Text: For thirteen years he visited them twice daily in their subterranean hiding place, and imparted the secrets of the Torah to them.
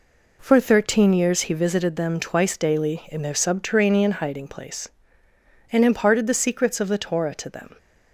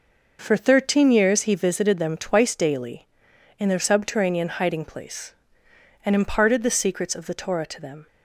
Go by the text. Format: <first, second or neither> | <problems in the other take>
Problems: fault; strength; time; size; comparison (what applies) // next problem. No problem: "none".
neither | none